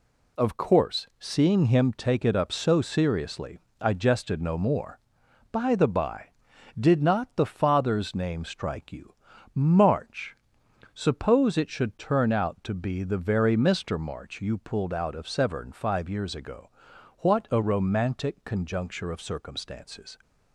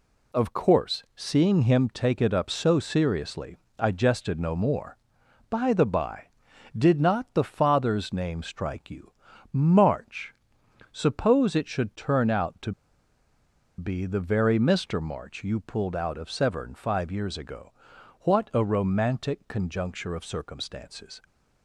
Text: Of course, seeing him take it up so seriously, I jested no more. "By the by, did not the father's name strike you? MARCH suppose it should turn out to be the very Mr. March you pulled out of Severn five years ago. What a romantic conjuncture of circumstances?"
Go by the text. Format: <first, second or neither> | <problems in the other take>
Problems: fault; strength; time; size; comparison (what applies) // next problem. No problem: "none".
first | pauses between "MARCH" and "suppose"; noticeable; at 10.3 s; 0.56 s long; noticeable in the first // pauses between "to" and "be"; at 12.7 s; 1.0 s long